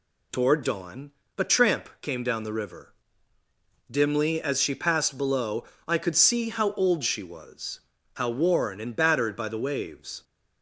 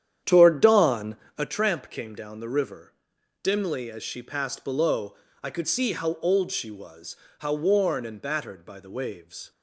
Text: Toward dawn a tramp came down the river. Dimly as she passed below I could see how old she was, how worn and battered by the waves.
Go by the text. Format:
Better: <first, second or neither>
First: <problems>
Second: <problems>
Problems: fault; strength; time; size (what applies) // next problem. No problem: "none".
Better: first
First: pauses between "dawn" and "a"; slight; at 1.1 s; 0.26 s long // pauses between "below" and "I"; slight; at 5.6 s; 0.24 s long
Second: starts louder than the rest; strong; until 1.5 s; 9.5 dB // pauses between "dawn" and "a"; slight; at 1.1 s; 0.20 s long // pauses between "below" and "I"; slight; at 5.1 s; 0.28 s long